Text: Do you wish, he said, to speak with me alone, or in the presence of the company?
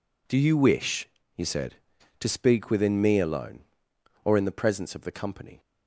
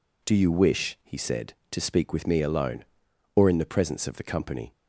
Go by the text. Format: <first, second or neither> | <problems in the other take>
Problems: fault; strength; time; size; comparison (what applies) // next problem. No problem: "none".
second | says "within" for "with"; at 2.6 s